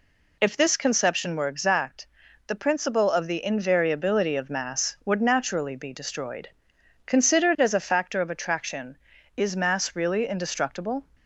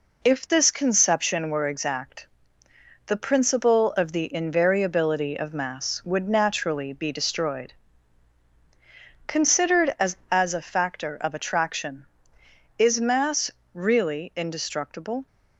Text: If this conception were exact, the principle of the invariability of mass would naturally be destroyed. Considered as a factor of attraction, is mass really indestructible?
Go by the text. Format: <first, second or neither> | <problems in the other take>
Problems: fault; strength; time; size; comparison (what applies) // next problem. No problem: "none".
first | says "as" twice; at 10.3 s // pauses between "mass" and "really"; slight; at 13.5 s; 0.24 s long